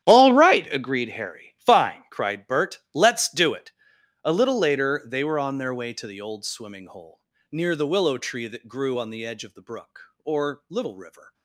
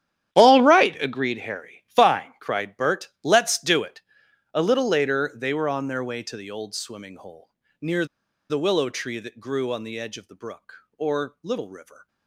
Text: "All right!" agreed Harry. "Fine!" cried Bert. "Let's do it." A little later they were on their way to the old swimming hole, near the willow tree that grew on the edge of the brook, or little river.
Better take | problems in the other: first | starts louder than the rest; strong; until 1.4 s; 10.5 dB; strong in the first // pauses between "near" and "the"; at 8.0 s; 0.44 s long

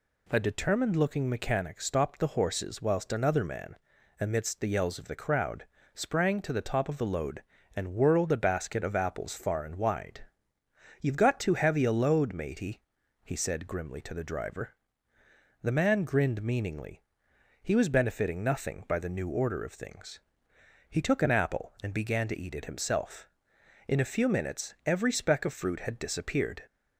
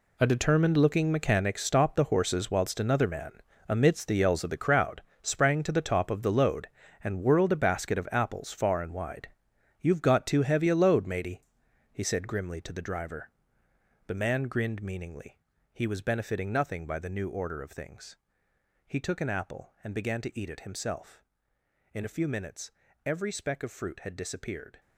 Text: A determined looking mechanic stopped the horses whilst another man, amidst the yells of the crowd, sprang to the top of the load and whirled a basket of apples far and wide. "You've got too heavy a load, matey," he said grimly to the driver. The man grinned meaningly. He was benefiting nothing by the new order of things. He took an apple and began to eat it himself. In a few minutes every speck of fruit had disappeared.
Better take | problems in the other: first | gets quieter; strong; throughout; 13.5 dB // pauses between "minutes" and "every"; slight; at 22.7 s; 0.34 s long

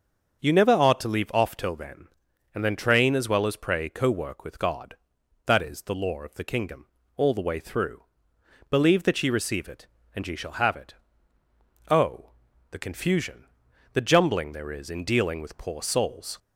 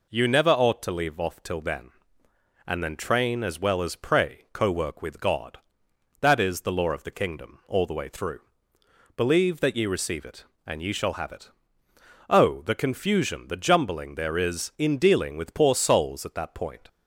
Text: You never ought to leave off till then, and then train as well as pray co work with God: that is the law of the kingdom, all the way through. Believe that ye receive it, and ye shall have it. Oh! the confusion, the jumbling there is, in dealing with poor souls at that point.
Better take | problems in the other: second | starts louder than the rest; until 1.4 s; 6.5 dB // stops before "at that point"; at 16.3 s

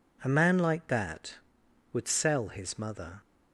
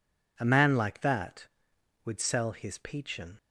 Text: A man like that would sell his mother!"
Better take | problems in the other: first | says "peachin" for "mother"; at 2.7 s

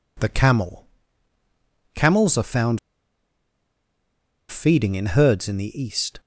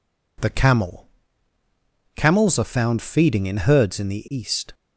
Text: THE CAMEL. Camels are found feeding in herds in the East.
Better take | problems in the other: second | pauses between "found" and "feeding"; strong; at 2.7 s; 1.7 s long

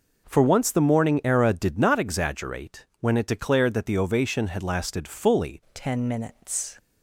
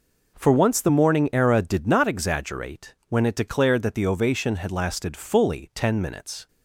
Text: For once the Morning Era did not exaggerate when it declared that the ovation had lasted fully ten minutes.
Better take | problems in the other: second | changes voice at "ten"; from 5.7 s on; 1.0 s long

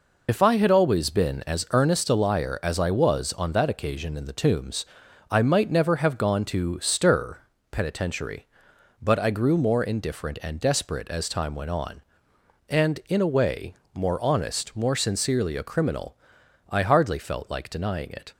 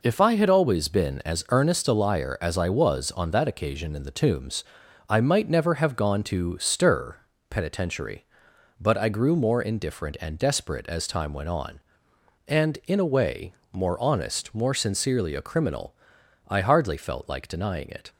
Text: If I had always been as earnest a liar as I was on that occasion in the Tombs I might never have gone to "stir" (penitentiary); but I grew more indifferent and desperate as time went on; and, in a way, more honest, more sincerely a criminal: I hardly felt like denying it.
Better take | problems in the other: second | loses the start of "If"; at 0.2 s; 55 ms // pauses between "Tombs" and "I"; at 4.8 s; 0.44 s long; also in the second

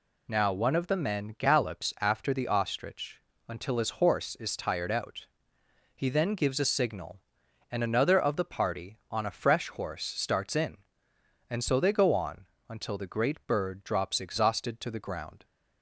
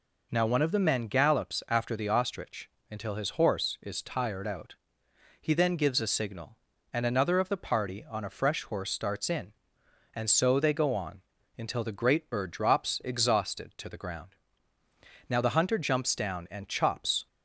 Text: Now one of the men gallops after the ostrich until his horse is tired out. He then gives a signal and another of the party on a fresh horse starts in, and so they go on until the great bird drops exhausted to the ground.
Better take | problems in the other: first | pauses between "ostrich" and "until"; slight; at 2.6 s; 0.22 s long; slight in the first // pauses between "on" and "until"; slight; at 11.2 s; 0.36 s long; slight in the first // goes on to say "Now the hunter jumps down and chops"; strong; from 15.2 s on; 1.9 s long

